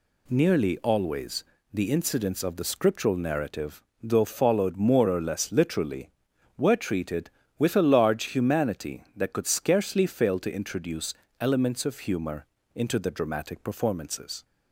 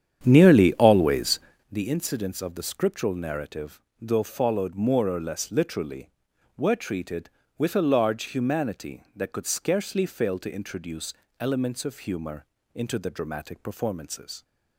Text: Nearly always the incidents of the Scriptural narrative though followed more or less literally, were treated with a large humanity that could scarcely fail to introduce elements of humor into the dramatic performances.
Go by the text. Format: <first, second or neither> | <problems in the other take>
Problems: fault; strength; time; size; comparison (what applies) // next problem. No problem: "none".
first | starts louder than the rest; strong; until 1.7 s; 9 dB // pauses between "always" and "the"; slight; at 1.3 s; 0.31 s long; slight in the first // pauses between "narrative" and "though"; slight; at 3.8 s; 0.18 s long; slight in the first // pauses between "introduce" and "elements"; slight; at 11.1 s; 0.26 s long; slight in the first // pauses between "humor" and "into"; slight; at 12.4 s; 0.30 s long; slight in the first